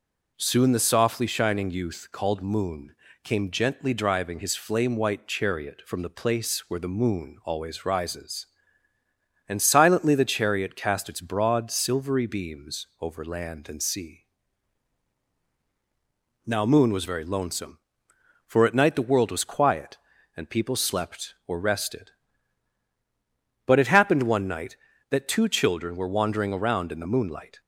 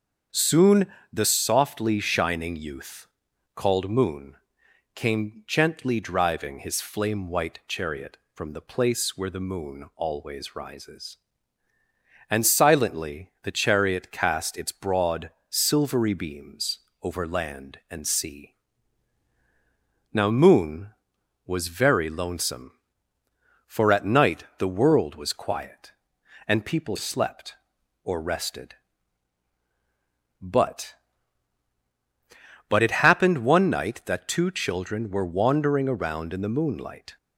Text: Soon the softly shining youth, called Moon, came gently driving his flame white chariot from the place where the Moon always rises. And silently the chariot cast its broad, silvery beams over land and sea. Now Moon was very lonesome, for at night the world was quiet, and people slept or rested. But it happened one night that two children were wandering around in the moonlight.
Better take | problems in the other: first | starts louder than the rest; until 1.5 s; 7 dB // pauses between "Soon" and "the"; slight; at 0.8 s; 0.26 s long // pauses between "beams" and "over"; slight; at 16.7 s; 0.22 s long // says "But" twice; at 32.6 s

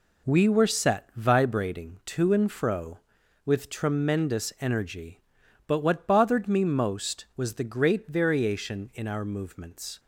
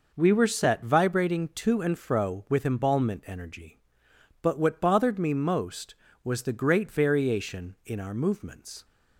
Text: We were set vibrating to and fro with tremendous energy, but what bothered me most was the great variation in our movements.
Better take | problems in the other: first | says "embalmment" for "tremendous"; at 2.6 s

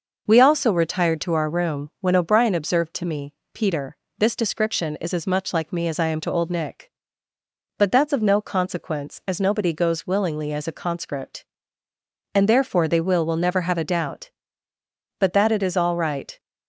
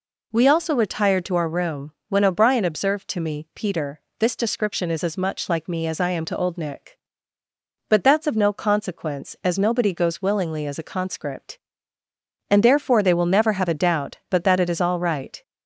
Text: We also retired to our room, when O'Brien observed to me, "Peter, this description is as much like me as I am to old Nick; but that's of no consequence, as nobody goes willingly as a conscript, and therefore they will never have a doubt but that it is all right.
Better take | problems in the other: second | says "will" twice; at 13.2 s

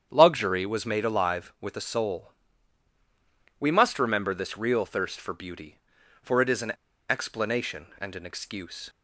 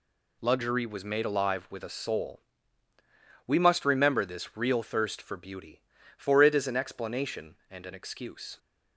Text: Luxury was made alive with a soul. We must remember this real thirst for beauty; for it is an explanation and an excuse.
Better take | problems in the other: second | starts louder than the rest; strong; until 1.1 s; 8.5 dB // pauses between "an" and "explanation"; at 6.7 s; 0.38 s long

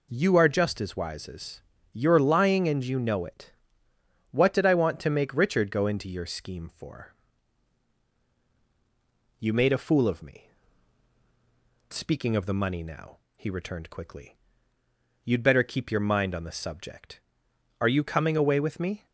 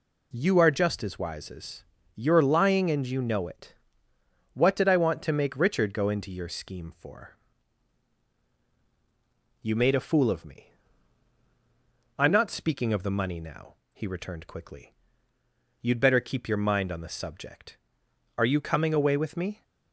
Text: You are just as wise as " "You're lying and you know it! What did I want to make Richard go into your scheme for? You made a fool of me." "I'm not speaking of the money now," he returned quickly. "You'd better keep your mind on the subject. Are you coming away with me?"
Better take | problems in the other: second | skips "I'm not"; at 11.2 s

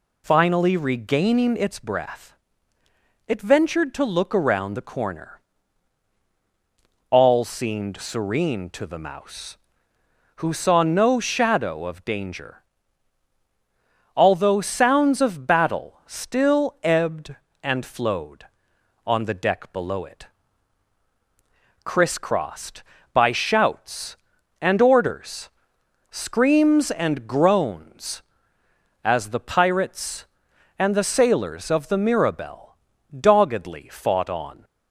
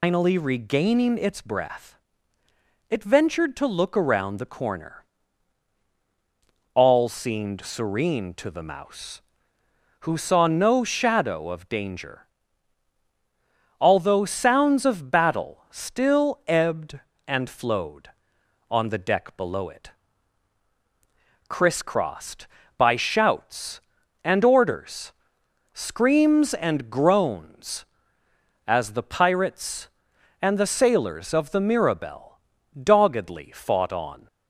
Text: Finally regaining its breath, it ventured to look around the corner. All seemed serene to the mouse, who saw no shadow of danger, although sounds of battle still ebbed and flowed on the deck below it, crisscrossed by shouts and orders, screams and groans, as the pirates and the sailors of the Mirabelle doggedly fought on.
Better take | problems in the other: first | loses the start of "Finally"; at 0.0 s; 165 ms // pauses between "Mirabelle" and "doggedly"; at 32.3 s; 0.44 s long; also in the first

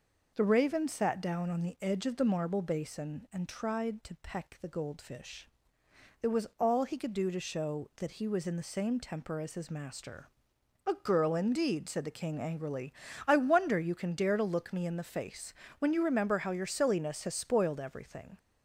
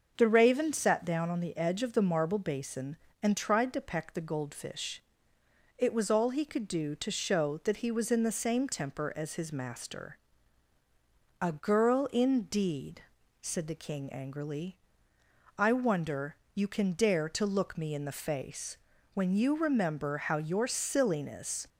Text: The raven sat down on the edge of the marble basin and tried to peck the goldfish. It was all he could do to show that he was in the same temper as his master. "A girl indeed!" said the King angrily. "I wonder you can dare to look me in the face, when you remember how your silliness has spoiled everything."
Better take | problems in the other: first | starts louder than the rest; until 1.2 s; 6.5 dB // pauses between "wonder" and "you"; slight; at 16.3 s; 0.16 s long // stops before "has spoiled everything"; at 21.6 s

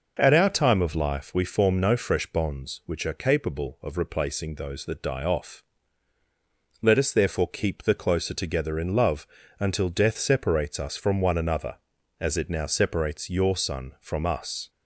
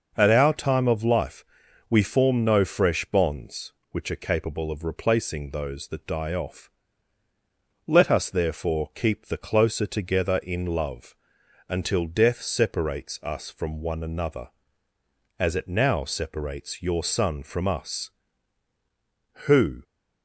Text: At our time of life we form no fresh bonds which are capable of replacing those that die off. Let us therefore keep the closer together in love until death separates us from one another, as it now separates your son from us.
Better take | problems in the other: first | pauses between "life" and "we"; noticeable; at 1.4 s; 0.46 s long // pauses between "love" and "until"; noticeable; at 11.1 s; 0.52 s long; slight in the first // goes on to say "Who"; slight; from 19.4 s on; 0.36 s long

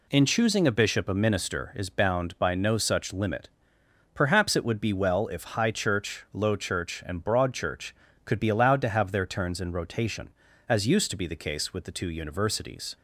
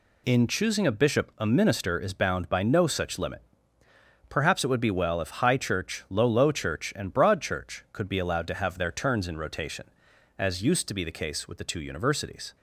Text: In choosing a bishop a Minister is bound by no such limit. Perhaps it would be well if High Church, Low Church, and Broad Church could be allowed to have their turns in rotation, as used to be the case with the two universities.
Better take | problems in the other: first | says "Low" twice; at 6.2 s

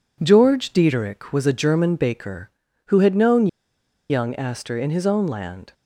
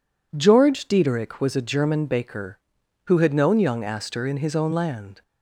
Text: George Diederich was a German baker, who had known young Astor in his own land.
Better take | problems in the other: second | pauses between "known" and "young"; noticeable; at 3.4 s; 0.62 s long

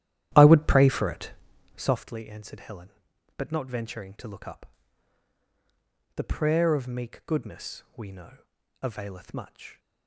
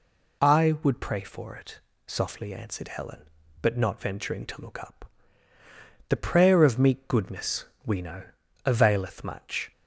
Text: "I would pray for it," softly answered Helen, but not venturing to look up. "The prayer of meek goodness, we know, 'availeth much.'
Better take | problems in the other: second | starts louder than the rest; strong; until 2.0 s; 12 dB

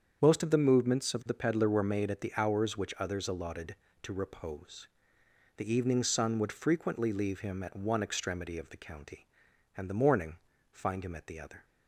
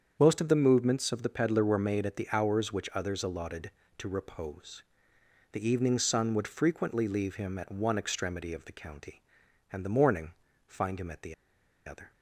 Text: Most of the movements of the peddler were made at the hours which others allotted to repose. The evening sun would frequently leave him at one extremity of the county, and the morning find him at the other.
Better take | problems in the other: first | starts louder than the rest; strong; until 1.2 s; 7.5 dB; strong in the first // pauses between "morning" and "find"; slight; at 10.3 s; 0.34 s long; slight in the first // pauses between "the" and "other"; noticeable; at 11.3 s; 0.52 s long

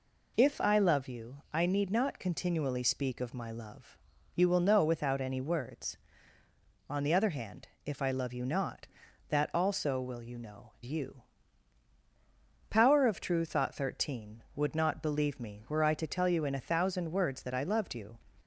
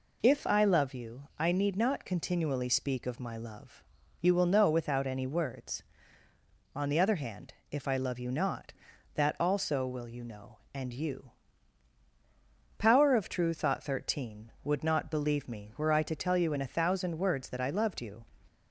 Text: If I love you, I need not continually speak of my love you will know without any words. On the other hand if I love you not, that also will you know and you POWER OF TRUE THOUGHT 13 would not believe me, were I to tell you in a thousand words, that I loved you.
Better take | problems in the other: second | pauses between "love" and "you"; at 3.9 s; 0.40 s long; also in the second // pauses between "hand" and "if"; slight; at 7.6 s; 0.18 s long; slight in the second // skips "and"; at 10.7 s // pauses between "you" and "POWER"; strong; at 11.2 s; 1.4 s long; strong in the second

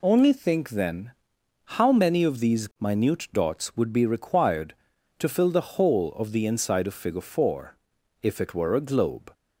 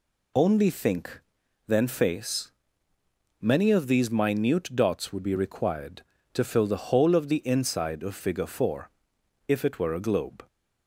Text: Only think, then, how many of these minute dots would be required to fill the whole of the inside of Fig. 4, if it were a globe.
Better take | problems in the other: first | says "face" for "how"; at 1.8 s

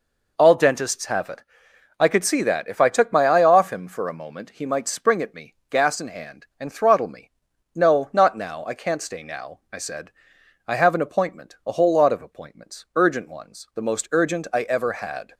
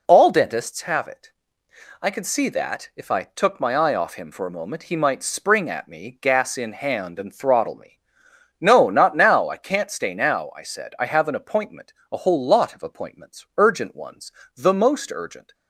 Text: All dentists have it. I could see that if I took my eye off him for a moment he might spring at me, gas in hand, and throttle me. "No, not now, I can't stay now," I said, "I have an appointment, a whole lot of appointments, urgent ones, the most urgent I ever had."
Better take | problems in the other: first | stops before "I ever had"; at 15.5 s

